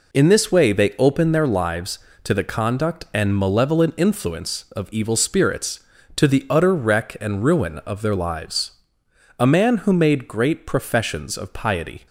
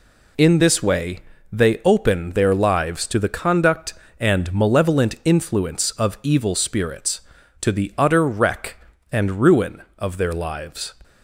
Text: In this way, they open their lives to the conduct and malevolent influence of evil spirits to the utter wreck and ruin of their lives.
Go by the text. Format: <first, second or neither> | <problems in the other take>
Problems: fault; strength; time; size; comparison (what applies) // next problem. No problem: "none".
second | goes on to say "A man who made great professions of piety"; strong; from 9.3 s on; 2.6 s long